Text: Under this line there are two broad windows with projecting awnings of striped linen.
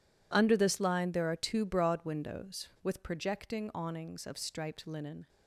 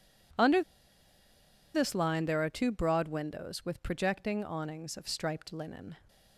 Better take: first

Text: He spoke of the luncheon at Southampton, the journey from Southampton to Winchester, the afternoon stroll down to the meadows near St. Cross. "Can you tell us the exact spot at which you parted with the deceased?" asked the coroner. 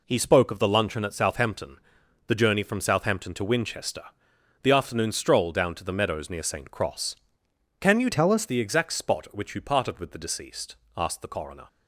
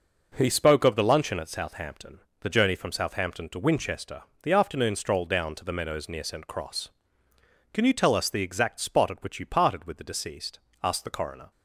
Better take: second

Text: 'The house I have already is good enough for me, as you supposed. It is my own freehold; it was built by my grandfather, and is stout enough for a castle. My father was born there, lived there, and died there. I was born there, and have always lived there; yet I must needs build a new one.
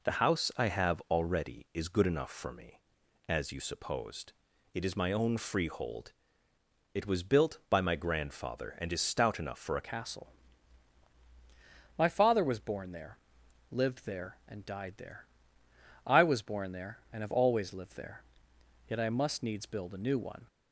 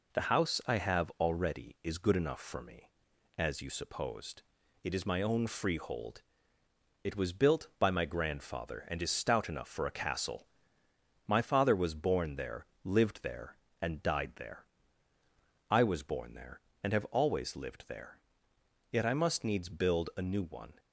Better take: second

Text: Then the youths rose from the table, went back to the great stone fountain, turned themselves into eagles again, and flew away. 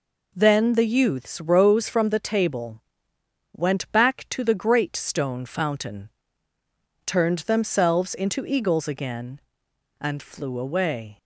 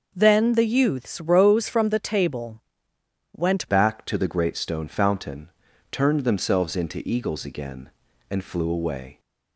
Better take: first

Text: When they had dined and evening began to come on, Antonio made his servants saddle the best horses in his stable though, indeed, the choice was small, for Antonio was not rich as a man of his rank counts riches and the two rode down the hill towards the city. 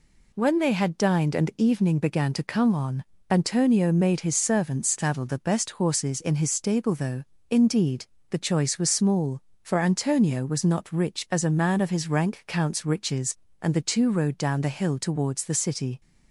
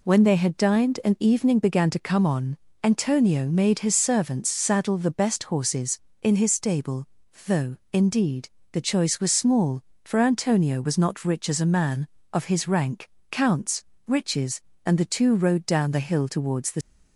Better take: first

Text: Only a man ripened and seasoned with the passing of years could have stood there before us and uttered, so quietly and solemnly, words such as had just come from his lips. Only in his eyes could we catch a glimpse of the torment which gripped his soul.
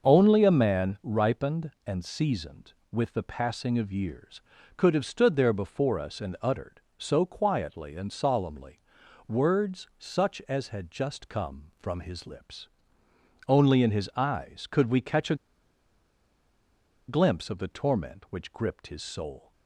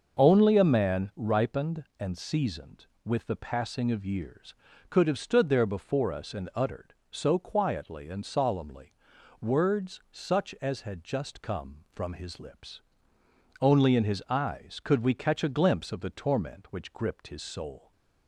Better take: second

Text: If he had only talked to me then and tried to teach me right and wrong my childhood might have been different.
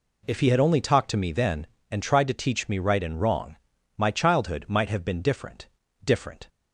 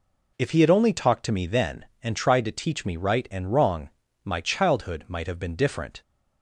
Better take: second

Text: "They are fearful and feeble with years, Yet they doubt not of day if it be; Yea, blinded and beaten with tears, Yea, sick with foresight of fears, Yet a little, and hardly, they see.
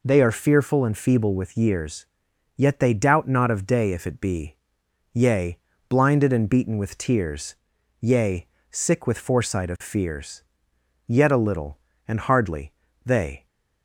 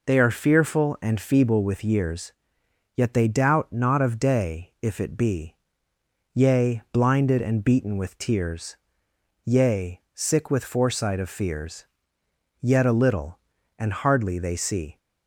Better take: second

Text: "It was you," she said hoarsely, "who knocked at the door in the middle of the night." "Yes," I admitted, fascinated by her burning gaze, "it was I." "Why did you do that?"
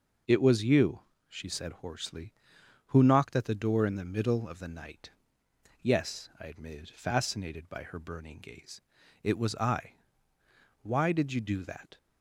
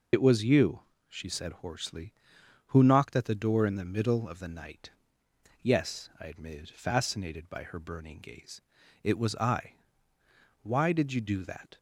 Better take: first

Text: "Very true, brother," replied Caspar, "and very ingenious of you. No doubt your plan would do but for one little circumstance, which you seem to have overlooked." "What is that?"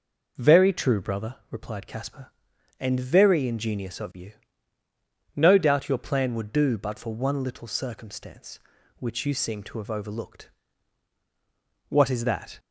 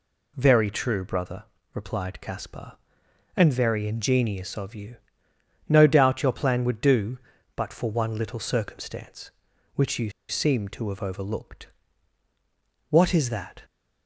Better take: first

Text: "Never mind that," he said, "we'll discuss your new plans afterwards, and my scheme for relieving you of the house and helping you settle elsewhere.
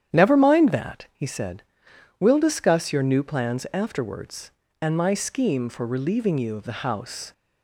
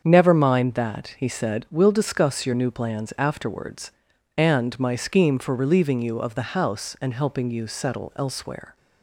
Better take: second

